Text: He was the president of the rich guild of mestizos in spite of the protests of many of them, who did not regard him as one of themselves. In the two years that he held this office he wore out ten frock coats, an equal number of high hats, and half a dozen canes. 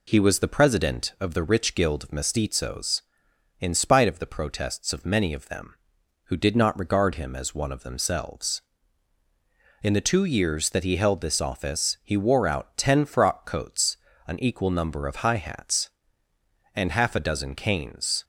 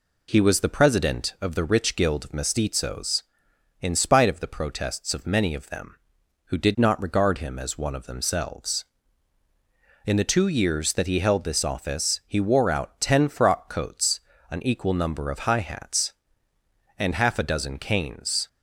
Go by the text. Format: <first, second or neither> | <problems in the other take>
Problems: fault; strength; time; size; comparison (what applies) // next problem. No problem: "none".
neither | none